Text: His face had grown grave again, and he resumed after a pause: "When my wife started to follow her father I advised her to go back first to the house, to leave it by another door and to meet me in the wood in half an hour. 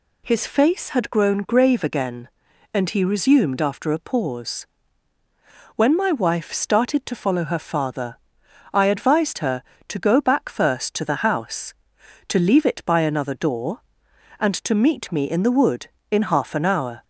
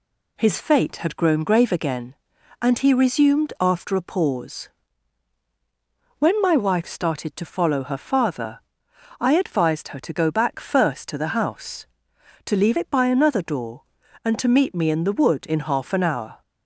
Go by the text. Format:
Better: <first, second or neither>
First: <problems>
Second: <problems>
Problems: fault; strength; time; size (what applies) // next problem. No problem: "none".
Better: first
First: pauses between "father" and "I"; noticeable; at 8.1 s; 0.56 s long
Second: says "fate" for "face"; at 0.6 s // pauses between "father" and "I"; noticeable; at 8.6 s; 0.58 s long